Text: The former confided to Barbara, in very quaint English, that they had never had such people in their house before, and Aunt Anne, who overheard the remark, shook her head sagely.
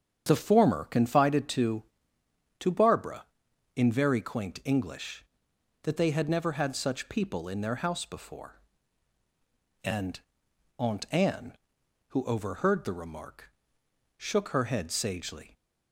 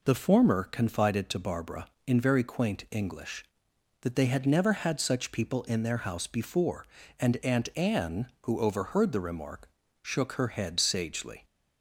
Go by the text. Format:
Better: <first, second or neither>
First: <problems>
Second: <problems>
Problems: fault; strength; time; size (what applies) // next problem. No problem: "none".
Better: second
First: starts louder than the rest; strong; until 1.3 s; 8 dB // says "to" twice; at 2.5 s // pauses between "and" and "Aunt"; noticeable; at 10.1 s; 0.58 s long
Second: none